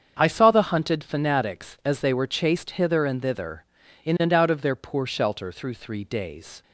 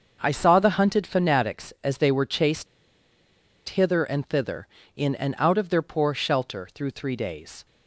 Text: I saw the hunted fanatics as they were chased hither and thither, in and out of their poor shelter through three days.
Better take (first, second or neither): first